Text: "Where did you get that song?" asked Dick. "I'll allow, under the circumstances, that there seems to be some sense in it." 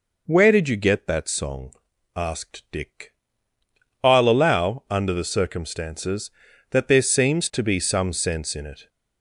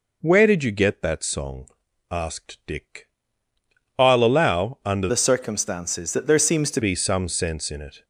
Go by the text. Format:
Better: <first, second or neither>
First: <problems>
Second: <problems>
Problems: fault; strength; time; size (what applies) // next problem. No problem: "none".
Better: first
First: none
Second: changes voice from "the" to "to"; from 5.0 to 6.8 s; 1.8 s long